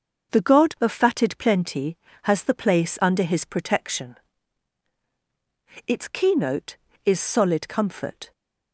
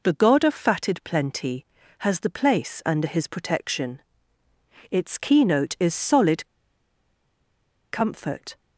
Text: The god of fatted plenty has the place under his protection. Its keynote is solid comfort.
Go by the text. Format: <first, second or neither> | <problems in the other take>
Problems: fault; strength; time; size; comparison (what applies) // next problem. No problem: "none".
first | pauses between "solid" and "comfort"; strong; at 6.4 s; 1.4 s long